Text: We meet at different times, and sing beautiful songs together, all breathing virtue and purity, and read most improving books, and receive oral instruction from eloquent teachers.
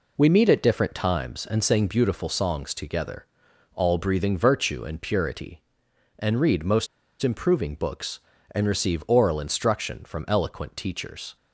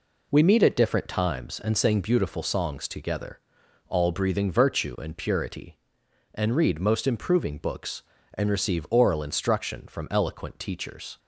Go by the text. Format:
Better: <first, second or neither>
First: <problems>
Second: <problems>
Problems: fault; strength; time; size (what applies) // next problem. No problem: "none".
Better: second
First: pauses between "most" and "improving"; slight; at 6.8 s; 0.35 s long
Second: none